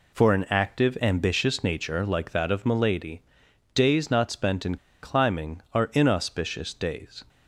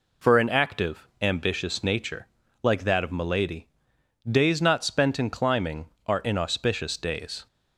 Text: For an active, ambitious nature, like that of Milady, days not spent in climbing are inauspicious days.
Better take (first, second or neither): second